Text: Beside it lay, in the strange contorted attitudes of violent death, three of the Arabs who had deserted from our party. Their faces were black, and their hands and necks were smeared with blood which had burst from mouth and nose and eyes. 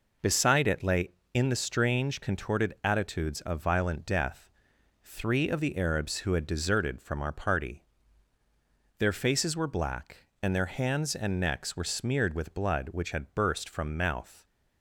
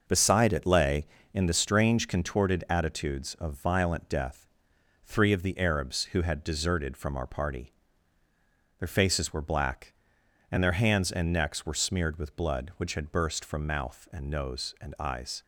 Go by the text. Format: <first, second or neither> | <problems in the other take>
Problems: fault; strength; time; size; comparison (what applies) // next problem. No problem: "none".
second | stops before "and nose and eyes"; at 14.4 s